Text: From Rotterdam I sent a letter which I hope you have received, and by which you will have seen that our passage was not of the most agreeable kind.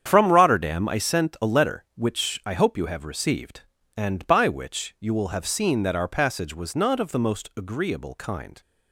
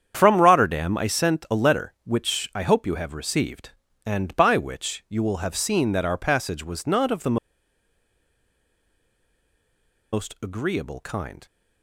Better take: first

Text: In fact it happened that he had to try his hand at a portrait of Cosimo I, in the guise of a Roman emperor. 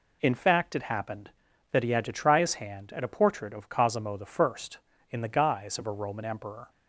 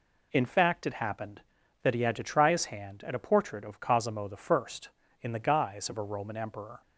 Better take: neither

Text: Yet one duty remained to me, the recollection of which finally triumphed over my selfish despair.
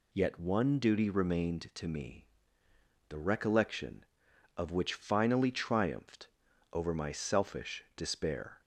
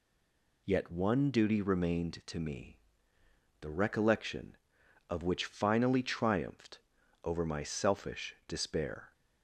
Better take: first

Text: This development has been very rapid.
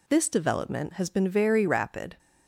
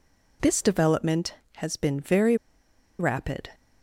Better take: first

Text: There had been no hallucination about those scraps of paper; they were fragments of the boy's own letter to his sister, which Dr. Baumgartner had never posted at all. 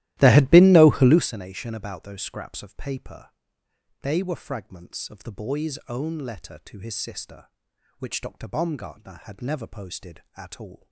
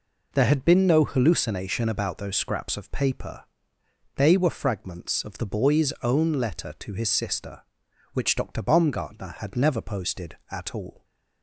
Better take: second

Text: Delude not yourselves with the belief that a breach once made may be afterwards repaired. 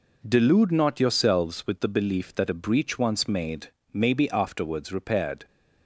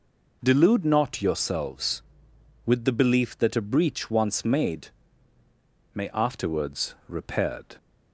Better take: first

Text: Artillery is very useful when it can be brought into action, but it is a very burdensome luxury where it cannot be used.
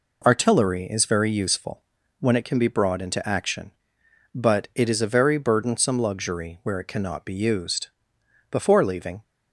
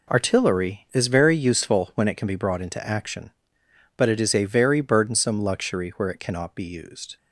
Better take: second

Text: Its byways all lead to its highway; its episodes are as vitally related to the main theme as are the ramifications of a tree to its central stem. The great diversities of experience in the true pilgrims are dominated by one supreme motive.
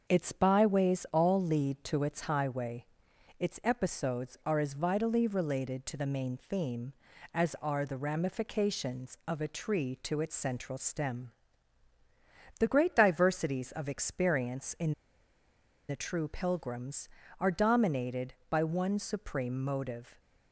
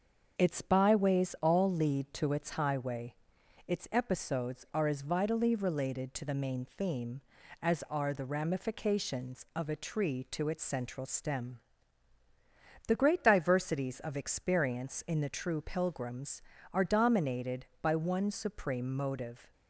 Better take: second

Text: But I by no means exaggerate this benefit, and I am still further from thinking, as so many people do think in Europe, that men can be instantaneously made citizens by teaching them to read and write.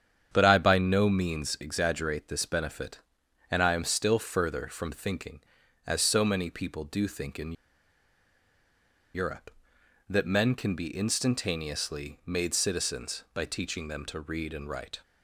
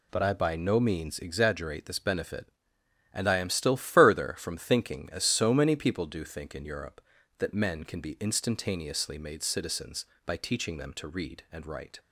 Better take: second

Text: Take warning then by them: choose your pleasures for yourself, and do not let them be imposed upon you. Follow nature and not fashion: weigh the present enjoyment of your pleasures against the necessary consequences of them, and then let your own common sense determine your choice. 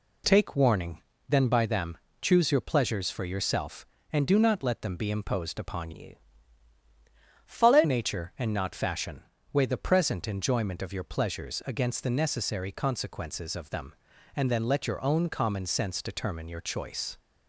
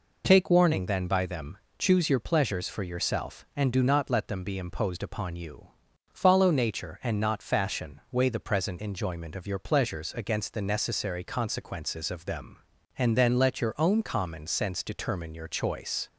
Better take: second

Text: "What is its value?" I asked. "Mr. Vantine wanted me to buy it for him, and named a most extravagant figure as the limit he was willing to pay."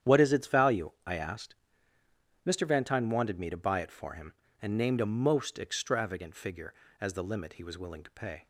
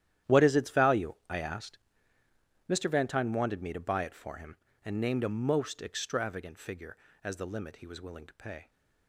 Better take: first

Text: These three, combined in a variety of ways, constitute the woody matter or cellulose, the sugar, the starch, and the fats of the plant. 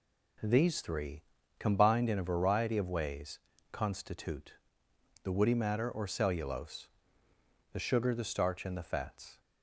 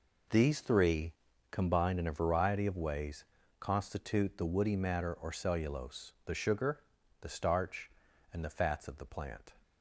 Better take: second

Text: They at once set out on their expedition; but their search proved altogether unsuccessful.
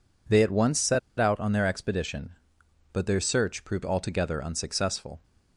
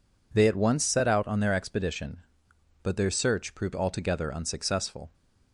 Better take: second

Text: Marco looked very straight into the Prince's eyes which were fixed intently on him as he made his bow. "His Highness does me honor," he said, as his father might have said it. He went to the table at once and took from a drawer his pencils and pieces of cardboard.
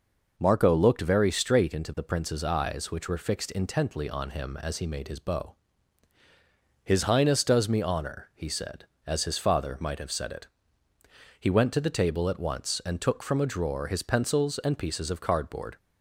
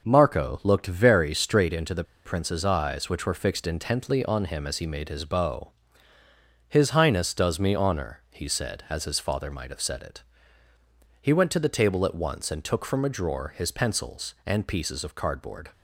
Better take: first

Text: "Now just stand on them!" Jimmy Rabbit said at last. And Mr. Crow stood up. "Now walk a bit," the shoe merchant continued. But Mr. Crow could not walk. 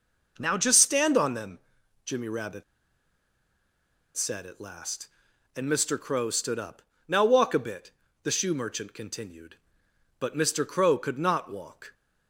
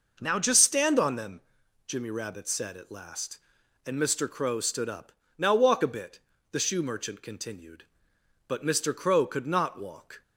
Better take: second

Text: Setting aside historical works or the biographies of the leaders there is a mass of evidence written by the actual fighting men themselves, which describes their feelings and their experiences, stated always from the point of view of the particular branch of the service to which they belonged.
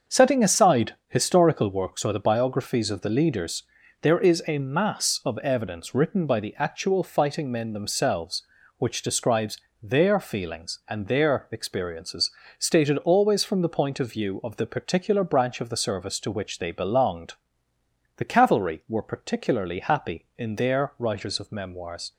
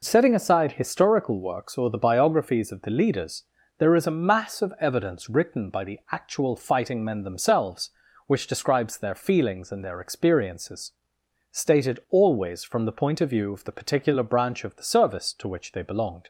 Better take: second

